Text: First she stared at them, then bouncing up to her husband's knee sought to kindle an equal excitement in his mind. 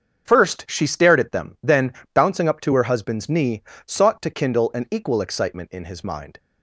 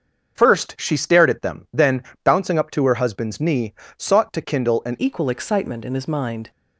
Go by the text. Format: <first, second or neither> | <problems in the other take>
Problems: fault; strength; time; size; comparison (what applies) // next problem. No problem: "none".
first | starts louder than the rest; until 1.4 s; 6.5 dB; also in the first // pauses between "then" and "bouncing"; slight; at 2.0 s; 0.20 s long; slight in the first // pauses between "knee" and "sought"; slight; at 3.7 s; 0.24 s long; slight in the first // changes voice at "equal"; from 5.0 s on; 1.5 s long